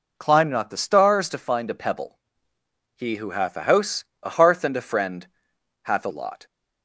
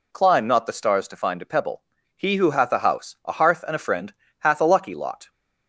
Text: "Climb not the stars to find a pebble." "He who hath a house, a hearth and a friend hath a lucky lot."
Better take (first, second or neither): second